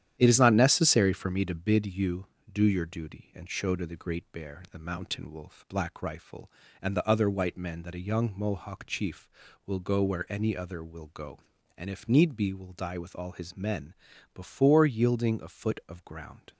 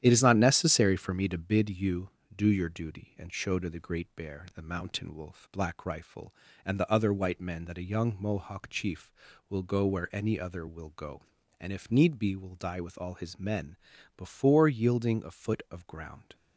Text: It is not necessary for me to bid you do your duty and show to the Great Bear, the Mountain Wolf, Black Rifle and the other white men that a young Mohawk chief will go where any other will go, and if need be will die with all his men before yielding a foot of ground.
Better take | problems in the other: neither | starts louder than the rest; strong; the same in both // pauses between "men" and "before"; the same in both

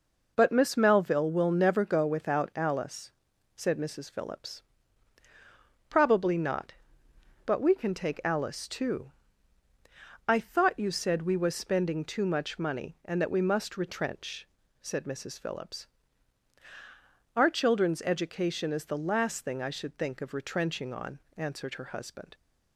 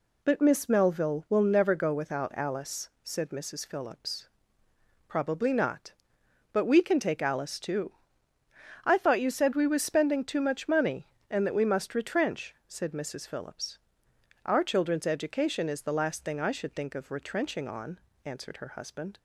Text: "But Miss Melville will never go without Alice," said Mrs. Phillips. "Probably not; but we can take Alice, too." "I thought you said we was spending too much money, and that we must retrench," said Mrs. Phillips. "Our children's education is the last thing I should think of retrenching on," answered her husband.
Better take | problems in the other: neither | none

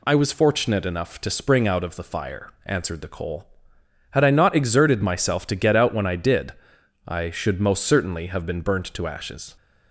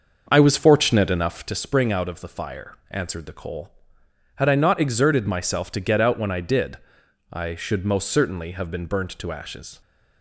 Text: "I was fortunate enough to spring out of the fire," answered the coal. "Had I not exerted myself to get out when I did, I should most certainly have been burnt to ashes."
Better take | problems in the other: first | starts louder than the rest; until 1.5 s; 6 dB

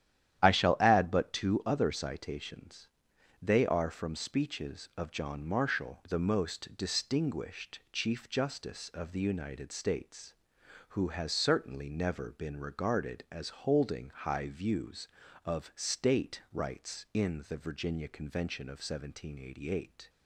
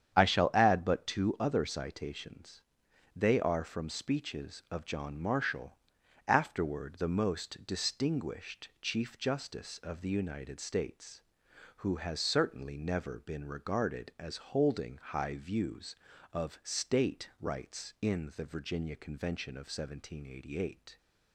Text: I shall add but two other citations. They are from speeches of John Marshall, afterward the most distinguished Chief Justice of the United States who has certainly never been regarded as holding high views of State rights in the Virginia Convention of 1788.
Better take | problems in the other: second | starts louder than the rest; strong; until 1.4 s; 11 dB; strong in the second // skips "afterward"; at 6.0 s // pauses between "as" and "holding"; slight; at 13.4 s; 0.16 s long; slight in the second

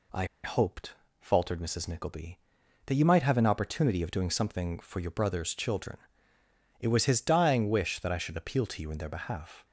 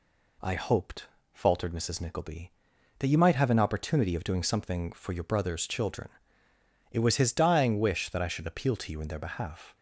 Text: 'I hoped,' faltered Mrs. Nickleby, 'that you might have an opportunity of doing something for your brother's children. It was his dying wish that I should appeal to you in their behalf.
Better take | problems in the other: second | pauses between "I" and "hoped"; slight; at 0.2 s; 0.18 s long

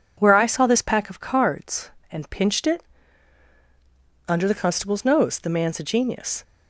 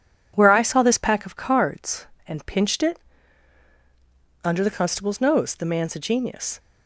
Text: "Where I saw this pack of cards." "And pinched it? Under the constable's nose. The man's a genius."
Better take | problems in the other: first | gets quieter; noticeable; throughout; 4 dB

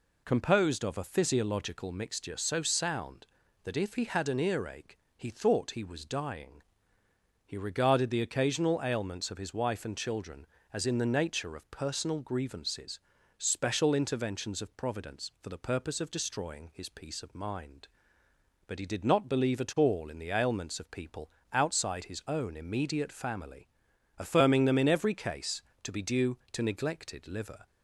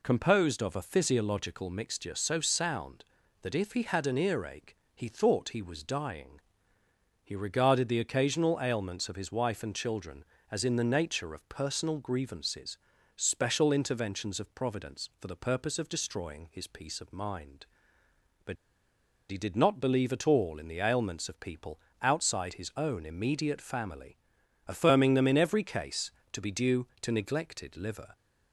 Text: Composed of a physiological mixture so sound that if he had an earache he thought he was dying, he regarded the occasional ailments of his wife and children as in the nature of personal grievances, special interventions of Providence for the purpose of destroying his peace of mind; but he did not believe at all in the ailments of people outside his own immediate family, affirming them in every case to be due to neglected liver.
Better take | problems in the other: first | pauses between "earache" and "he"; slight; at 4.7 s; 0.20 s long; slight in the first // pauses between "but" and "he"; noticeable; at 18.5 s; 0.75 s long // pauses between "people" and "outside"; slight; at 21.7 s; 0.22 s long; slight in the first

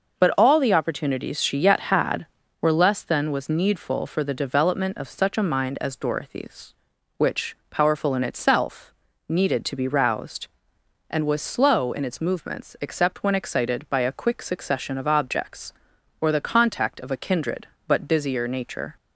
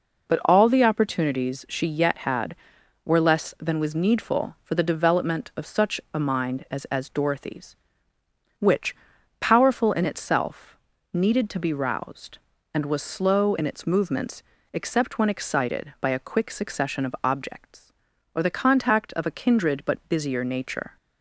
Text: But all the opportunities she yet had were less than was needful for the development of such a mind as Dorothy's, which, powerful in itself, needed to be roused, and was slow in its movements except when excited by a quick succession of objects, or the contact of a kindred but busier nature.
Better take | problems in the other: first | says "as" twice; at 6.8 s // pauses between "movements" and "except"; slight; at 14.4 s; 0.30 s long

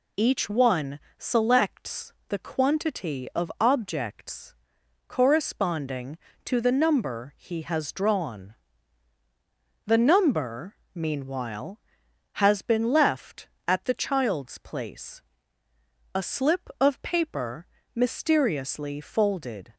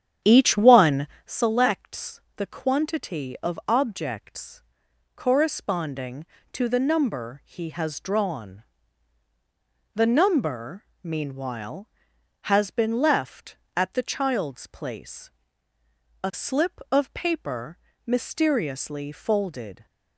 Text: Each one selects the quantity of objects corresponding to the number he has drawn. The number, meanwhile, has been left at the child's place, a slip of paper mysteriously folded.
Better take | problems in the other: first | starts louder than the rest; strong; until 1.4 s; 9 dB // pauses between "one" and "selects"; slight; at 1.0 s; 0.18 s long; slight in the first // pauses between "selects" and "the"; slight; at 2.2 s; 0.16 s long; slight in the first // pauses between "objects" and "corresponding"; noticeable; at 4.6 s; 0.52 s long; noticeable in the first // pauses between "paper" and "mysteriously"; slight; at 17.7 s; 0.28 s long; slight in the first

